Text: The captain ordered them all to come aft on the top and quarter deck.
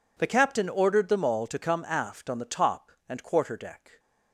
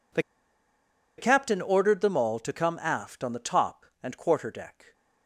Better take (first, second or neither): first